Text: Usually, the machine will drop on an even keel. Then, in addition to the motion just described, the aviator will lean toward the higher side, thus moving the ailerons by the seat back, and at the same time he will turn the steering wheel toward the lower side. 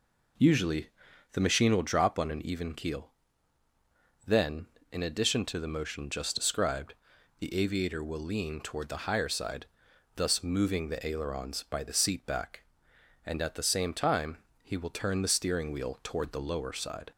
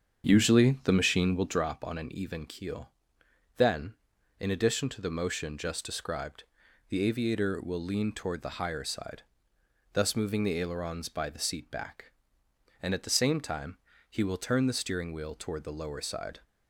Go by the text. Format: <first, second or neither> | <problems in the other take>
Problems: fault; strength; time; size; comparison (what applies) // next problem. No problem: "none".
first | starts louder than the rest; strong; until 1.7 s; 7.5 dB // pauses between "time" and "he"; slight; at 13.7 s; 0.32 s long; slight in the first